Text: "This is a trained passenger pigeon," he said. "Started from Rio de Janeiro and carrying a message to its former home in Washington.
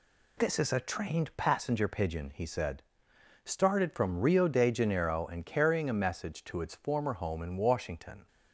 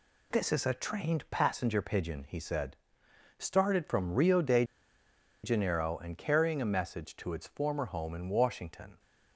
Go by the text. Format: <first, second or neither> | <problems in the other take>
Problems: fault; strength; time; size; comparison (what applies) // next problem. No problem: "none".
first | pauses between "de" and "Janeiro"; noticeable; at 4.6 s; 0.80 s long